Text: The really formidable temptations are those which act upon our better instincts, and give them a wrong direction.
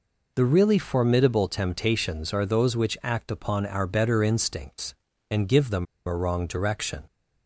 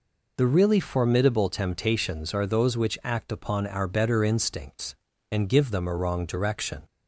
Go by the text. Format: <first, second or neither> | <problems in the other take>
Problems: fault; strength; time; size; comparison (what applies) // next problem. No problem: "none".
second | pauses between "them" and "a"; slight; at 5.8 s; 0.23 s long